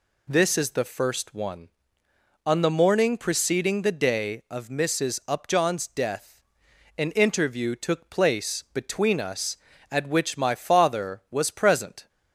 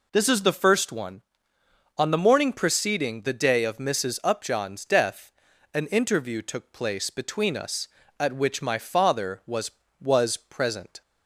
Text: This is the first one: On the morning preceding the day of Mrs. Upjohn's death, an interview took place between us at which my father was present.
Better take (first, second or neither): first